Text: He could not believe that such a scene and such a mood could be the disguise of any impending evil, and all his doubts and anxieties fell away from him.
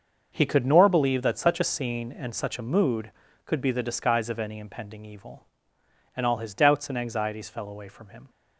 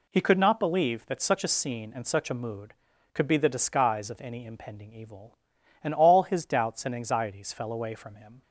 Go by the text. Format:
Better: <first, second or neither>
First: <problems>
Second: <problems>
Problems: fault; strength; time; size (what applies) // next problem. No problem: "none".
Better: second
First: starts louder than the rest; until 1.3 s; 6.5 dB // says "nor" for "not"; at 0.6 s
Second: none